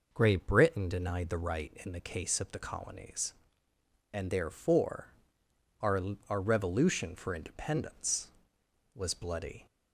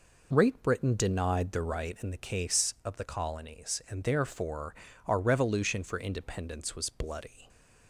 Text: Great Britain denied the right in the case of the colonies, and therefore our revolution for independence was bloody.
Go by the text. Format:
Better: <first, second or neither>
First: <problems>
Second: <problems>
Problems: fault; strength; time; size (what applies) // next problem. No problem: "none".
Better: second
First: pauses between "therefore" and "our"; noticeable; at 5.1 s; 0.68 s long // says "our" twice; at 6.2 s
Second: pauses between "therefore" and "our"; slight; at 4.7 s; 0.32 s long